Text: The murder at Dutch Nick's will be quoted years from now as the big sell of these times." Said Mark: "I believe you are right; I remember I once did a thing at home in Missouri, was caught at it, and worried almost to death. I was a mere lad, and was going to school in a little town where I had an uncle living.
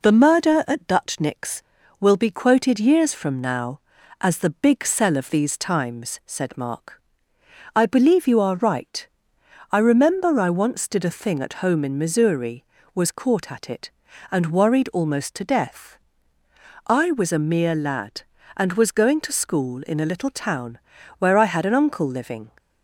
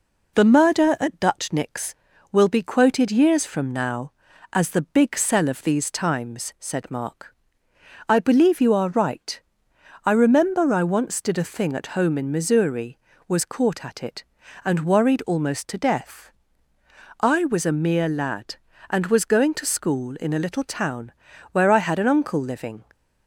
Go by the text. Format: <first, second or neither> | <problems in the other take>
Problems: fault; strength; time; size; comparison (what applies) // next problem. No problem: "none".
neither | pauses between "town" and "where"; the same in both